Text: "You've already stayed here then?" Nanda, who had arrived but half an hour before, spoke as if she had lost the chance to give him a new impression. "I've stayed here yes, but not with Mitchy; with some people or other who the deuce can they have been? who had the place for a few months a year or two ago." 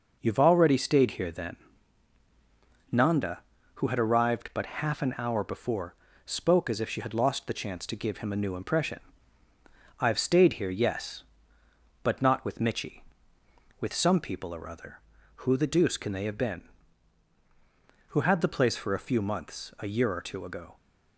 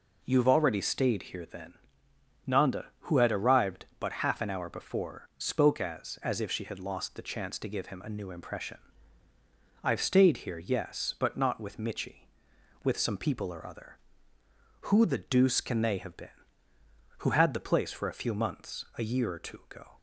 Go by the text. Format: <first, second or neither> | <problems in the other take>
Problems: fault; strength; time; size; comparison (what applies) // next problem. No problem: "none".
first | says "as" twice; at 6.2 s